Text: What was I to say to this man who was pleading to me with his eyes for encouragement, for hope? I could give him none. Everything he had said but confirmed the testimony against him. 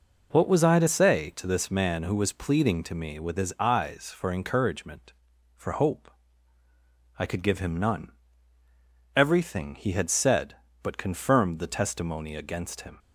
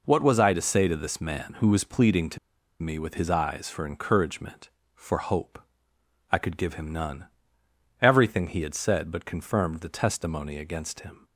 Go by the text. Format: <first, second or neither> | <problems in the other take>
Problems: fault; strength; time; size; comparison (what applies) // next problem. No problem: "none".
first | pauses between "to" and "me"; at 2.3 s; 0.44 s long